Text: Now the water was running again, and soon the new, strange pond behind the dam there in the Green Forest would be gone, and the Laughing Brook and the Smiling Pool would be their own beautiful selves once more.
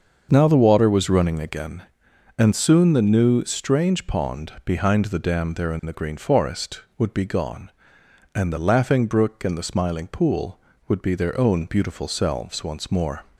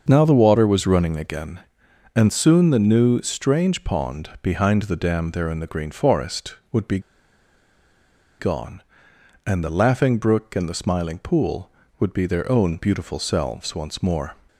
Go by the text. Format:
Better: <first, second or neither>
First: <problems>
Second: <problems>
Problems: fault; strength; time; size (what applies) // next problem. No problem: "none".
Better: first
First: starts louder than the rest; until 1.3 s; 6.5 dB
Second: starts louder than the rest; until 1.0 s; 6.5 dB // pauses between "be" and "gone"; strong; at 6.9 s; 1.4 s long